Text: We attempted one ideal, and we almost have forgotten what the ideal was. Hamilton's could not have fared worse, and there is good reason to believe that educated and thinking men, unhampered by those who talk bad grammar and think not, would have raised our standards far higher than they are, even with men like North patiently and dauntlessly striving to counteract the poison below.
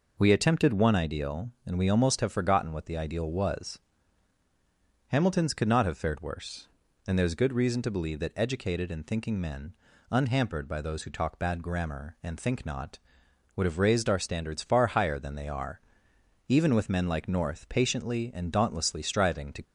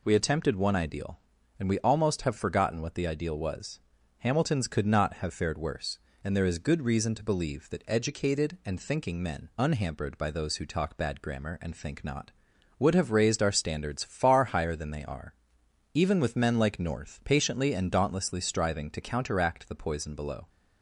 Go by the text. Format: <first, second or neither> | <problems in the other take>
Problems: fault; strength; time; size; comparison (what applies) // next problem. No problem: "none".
second | stops before "counteract the poison below"; at 19.6 s